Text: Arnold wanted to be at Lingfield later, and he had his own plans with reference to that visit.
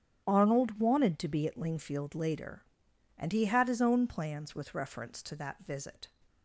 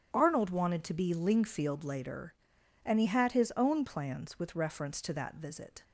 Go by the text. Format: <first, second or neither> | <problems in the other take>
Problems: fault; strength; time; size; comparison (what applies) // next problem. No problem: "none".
first | starts louder than the rest; strong; until 1.1 s; 8.5 dB; strong in the first // skips "at"; at 1.1 s